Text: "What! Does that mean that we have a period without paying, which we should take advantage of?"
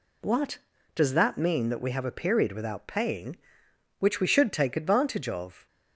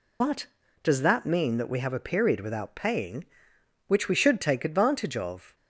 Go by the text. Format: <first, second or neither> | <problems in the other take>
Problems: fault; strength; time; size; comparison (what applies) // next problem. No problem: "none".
first | loses the start of "What"; at 0.2 s; 90 ms